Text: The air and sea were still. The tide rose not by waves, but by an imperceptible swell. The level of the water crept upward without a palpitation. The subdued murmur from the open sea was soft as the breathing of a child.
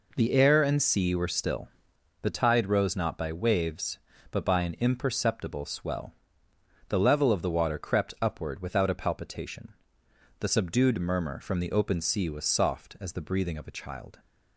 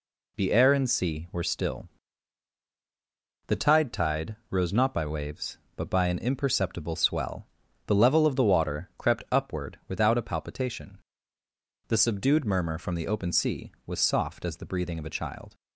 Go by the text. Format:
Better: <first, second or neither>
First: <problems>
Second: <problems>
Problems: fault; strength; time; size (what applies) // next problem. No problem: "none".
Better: first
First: none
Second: says "tide" twice; at 3.9 s